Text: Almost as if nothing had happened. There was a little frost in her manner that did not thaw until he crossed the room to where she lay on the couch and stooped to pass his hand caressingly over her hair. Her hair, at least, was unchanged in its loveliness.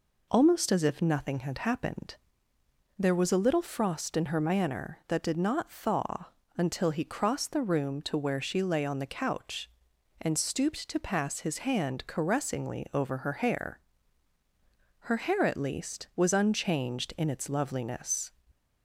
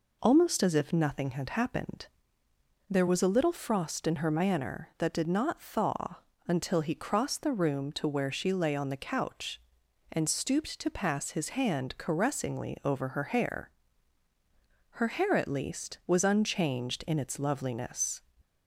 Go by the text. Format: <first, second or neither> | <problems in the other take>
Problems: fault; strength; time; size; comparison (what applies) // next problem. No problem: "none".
neither | pauses between "thaw" and "until"; slight; the same in both